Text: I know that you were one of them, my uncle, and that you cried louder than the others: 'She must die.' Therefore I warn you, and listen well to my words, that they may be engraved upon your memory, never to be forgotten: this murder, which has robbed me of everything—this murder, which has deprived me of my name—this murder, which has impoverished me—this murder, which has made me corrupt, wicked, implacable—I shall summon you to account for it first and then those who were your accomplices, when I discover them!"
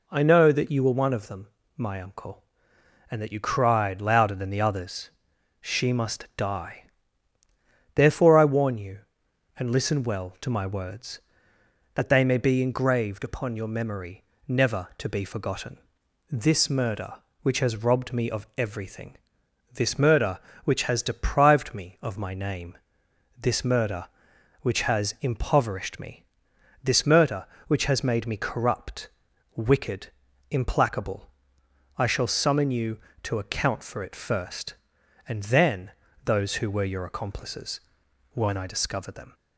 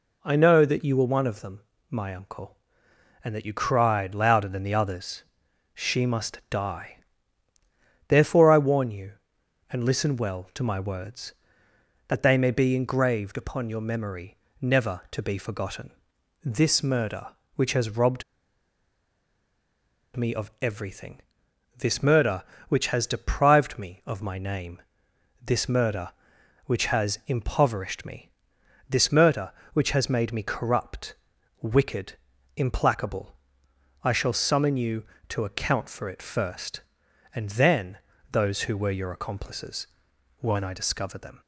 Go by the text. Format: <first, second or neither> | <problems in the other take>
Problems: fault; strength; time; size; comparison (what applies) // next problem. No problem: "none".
first | pauses between "robbed" and "me"; strong; at 18.2 s; 1.9 s long // pauses between "then" and "those"; slight; at 37.9 s; 0.32 s long; slight in the first